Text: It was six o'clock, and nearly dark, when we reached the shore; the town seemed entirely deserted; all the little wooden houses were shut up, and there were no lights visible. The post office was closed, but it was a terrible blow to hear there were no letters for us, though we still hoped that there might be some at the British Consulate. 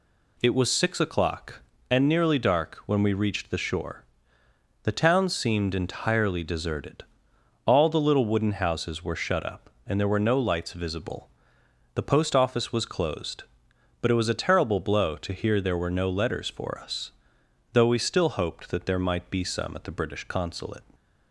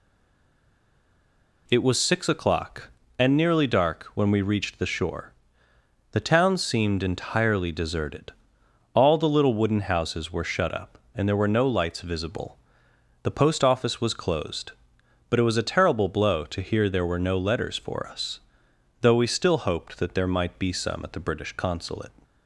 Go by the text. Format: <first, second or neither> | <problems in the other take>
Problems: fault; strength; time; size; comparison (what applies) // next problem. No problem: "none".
first | stays silent before the first word; noticeable; until 1.6 s; 1.6 s long